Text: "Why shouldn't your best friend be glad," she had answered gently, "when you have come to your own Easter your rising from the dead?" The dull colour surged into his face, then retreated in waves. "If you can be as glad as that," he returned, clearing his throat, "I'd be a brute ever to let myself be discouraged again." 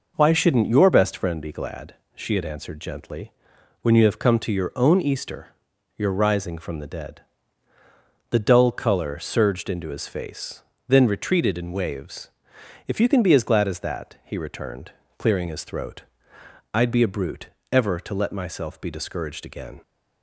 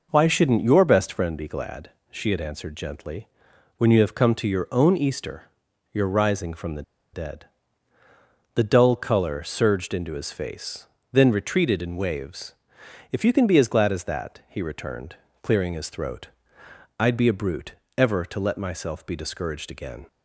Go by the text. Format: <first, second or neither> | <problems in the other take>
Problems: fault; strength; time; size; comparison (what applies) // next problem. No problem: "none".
first | pauses between "Easter" and "your"; at 5.5 s; 0.42 s long; also in the first // pauses between "the" and "dead"; slight; at 6.8 s; 0.30 s long // pauses between "brute" and "ever"; slight; at 17.7 s; 0.22 s long; slight in the first